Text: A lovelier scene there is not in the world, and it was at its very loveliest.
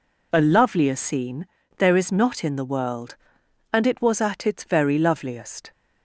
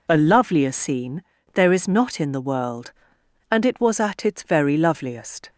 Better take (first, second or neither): neither